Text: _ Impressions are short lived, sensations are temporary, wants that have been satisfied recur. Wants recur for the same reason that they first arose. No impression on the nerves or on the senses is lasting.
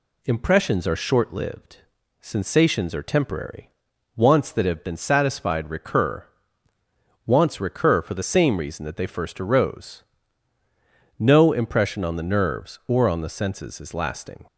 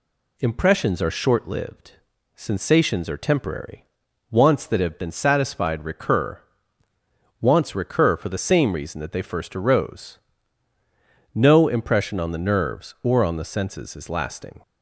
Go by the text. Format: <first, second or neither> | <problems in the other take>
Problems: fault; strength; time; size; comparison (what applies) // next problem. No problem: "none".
neither | none